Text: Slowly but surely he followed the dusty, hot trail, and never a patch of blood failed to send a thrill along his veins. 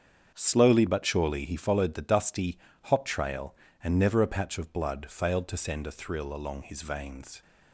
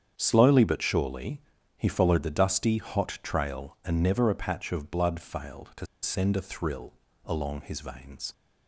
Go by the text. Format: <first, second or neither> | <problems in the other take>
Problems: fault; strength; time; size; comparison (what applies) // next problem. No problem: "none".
first | starts louder than the rest; strong; until 1.1 s; 8 dB; strong in the first // pauses between "surely" and "he"; slight; at 1.4 s; 0.34 s long // pauses between "to" and "send"; slight; at 5.8 s; 0.17 s long // pauses between "thrill" and "along"; slight; at 6.9 s; 0.32 s long